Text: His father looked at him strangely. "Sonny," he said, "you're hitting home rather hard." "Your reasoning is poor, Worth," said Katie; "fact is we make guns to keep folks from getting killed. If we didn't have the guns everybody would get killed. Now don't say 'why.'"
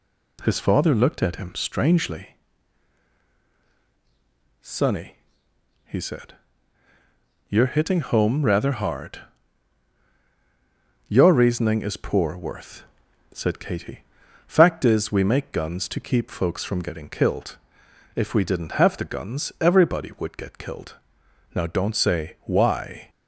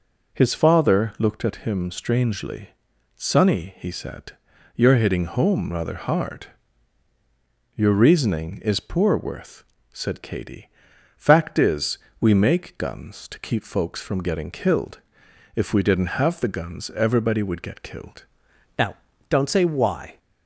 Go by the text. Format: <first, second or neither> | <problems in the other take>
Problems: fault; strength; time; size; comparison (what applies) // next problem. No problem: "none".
first | pauses between "is" and "we"; slight; at 11.9 s; 0.22 s long // changes voice at "Now"; from 18.7 s on; 1.4 s long // pauses between "Now" and "don't"; slight; at 18.9 s; 0.34 s long